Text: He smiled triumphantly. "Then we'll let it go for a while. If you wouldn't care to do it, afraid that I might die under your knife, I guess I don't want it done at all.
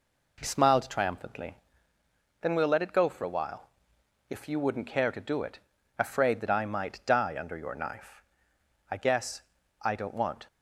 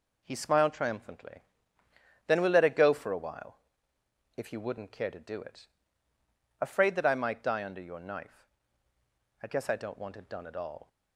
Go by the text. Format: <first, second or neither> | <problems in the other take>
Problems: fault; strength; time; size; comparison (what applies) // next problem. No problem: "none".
second | pauses between "guess" and "I"; at 9.4 s; 0.40 s long // stops before "it done at all"; at 10.4 s